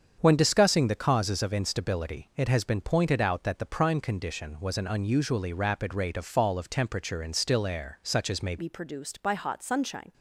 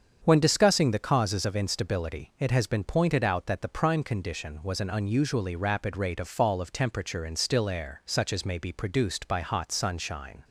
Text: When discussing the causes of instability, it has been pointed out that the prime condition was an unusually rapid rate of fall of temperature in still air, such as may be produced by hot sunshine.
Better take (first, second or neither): second